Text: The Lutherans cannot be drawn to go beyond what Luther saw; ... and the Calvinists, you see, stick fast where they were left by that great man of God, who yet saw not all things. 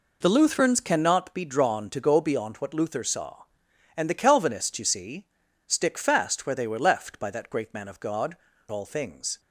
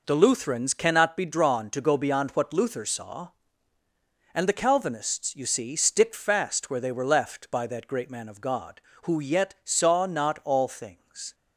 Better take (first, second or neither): second